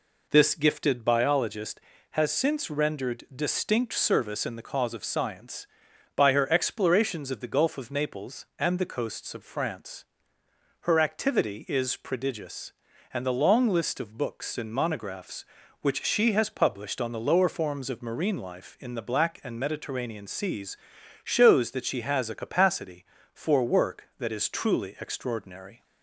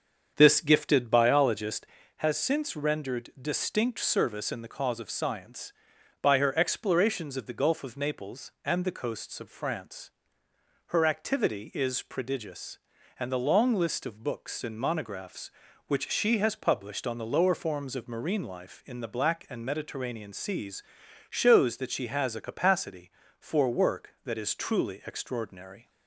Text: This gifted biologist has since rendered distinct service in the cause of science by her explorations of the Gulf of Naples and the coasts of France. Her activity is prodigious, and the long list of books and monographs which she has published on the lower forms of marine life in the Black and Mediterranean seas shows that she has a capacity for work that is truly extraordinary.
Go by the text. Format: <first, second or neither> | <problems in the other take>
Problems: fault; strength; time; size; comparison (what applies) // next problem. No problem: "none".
first | starts louder than the rest; until 2.2 s; 7 dB // pauses between "seas" and "shows"; noticeable; at 20.8 s; 0.48 s long; noticeable in the first